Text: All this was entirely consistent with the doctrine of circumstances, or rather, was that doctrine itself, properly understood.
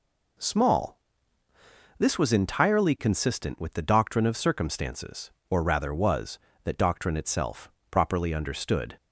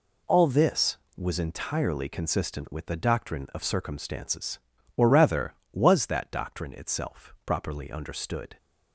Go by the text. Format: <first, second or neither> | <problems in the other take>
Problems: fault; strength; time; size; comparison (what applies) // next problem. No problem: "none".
second | says "Small" for "All"; at 0.3 s